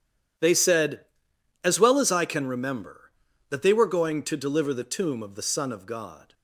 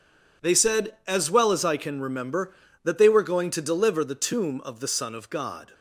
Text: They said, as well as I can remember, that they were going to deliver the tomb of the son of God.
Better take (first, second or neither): neither